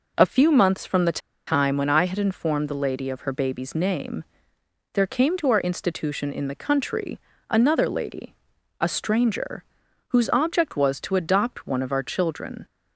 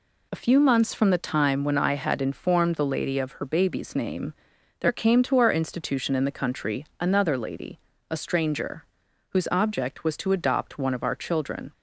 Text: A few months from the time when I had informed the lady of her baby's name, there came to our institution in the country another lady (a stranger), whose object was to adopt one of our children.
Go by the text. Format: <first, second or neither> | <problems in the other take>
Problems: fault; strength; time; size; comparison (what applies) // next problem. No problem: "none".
second | pauses between "the" and "time"; slight; at 1.1 s; 0.28 s long // pauses between "country" and "another"; slight; at 7.1 s; 0.32 s long